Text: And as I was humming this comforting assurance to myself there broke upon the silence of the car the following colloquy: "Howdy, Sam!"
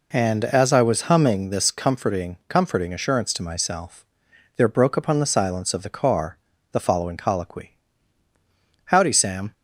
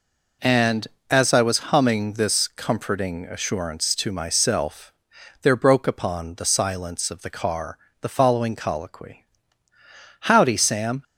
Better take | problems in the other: second | says "comforting" twice; at 2.4 s // pauses between "myself" and "there"; noticeable; at 4.0 s; 0.54 s long; noticeable in the second // pauses between "car" and "the"; at 6.3 s; 0.38 s long; slight in the second

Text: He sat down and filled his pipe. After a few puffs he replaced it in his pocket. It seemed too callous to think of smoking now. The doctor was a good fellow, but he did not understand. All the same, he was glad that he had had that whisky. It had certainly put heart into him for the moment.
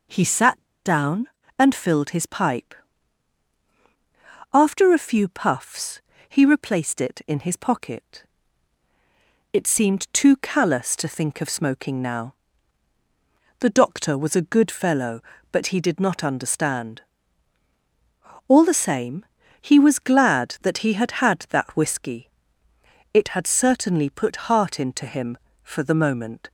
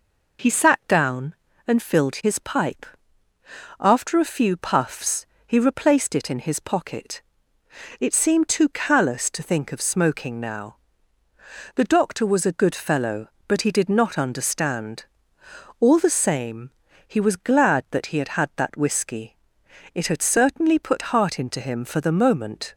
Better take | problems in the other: second | pauses between "sat" and "down"; slight; at 0.6 s; 0.23 s long // pauses between "puffs" and "he"; slight; at 6.0 s; 0.28 s long; slight in the second

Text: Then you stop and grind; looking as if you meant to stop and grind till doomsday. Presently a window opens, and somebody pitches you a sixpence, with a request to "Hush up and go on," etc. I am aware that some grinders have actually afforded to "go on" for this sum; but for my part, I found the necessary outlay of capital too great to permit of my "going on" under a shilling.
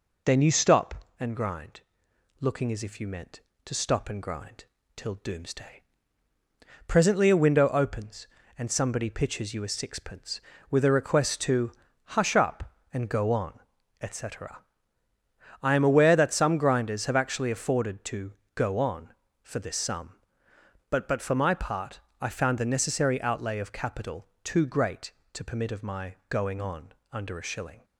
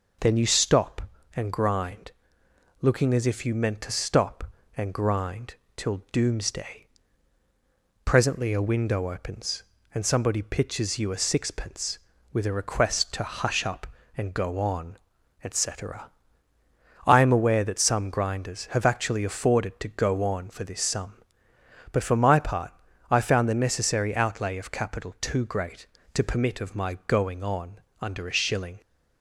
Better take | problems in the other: second | pauses between "grind" and "till"; slight; at 4.6 s; 0.30 s long; slight in the second // pauses between "to" and "Hush"; noticeable; at 11.7 s; 0.46 s long // pauses between "to" and "go"; slight; at 18.3 s; 0.22 s long // says "but" twice; at 21.0 s // pauses between "on" and "under"; slight; at 26.9 s; 0.18 s long; slight in the second

